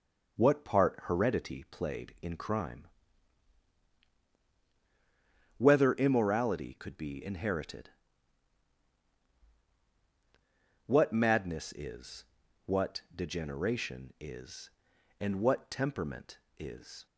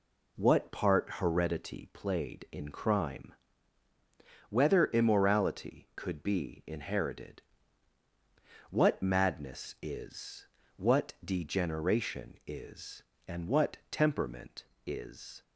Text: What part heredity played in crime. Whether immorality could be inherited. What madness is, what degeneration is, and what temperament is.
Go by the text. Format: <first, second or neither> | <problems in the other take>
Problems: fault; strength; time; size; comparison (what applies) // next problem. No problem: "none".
neither | none